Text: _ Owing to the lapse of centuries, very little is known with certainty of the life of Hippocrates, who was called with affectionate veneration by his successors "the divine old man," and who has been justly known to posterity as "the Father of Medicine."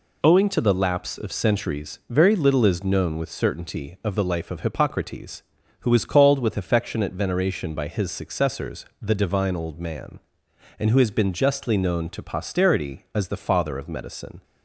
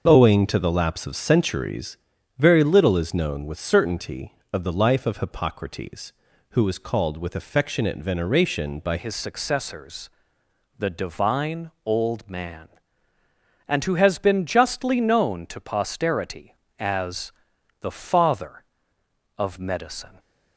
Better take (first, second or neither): first